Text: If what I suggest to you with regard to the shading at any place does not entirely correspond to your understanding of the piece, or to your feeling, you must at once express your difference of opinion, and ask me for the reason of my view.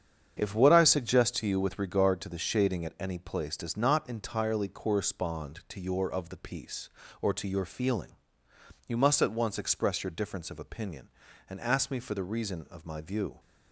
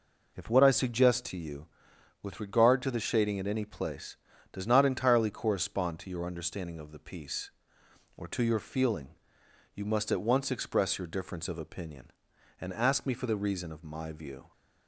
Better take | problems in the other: second | starts louder than the rest; strong; until 1.4 s; 8 dB // skips "understanding"; at 6.1 s

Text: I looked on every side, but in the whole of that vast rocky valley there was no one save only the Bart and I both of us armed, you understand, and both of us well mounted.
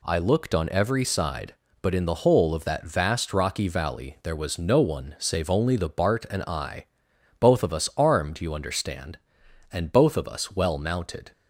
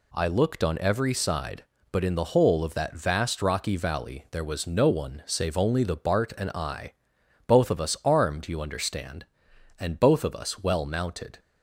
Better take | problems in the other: neither | pauses between "I" and "both"; noticeable; the same in both

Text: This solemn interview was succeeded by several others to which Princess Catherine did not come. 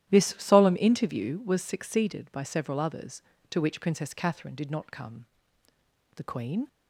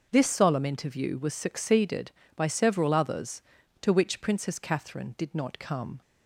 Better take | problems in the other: second | starts louder than the rest; strong; until 1.1 s; 12 dB; noticeable in the second // goes on to say "The queen"; from 6.1 s on; 0.52 s long

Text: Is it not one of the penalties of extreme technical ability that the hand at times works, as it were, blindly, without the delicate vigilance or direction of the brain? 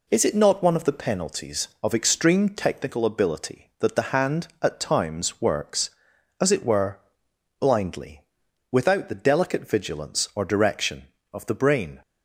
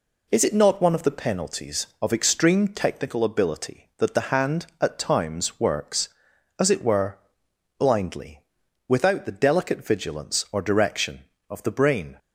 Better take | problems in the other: neither | none

